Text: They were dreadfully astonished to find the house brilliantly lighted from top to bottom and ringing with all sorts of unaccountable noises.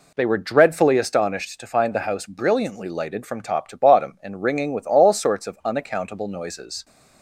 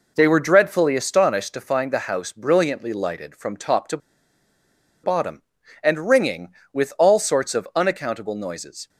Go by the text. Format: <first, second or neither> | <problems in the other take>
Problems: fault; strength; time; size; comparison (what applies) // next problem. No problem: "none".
first | pauses between "to" and "bottom"; at 3.9 s; 1.0 s long